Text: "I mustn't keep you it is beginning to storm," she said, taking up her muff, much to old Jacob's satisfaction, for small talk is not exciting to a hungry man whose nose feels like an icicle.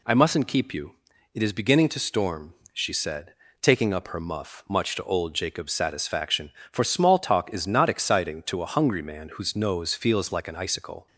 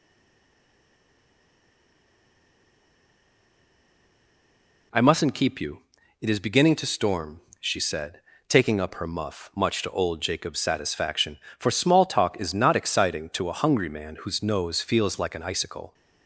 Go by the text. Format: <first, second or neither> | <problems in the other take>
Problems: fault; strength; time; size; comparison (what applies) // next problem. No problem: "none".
first | stays silent before the first word; strong; until 4.9 s; 4.9 s long // pauses between "you" and "it"; at 5.8 s; 0.38 s long; also in the first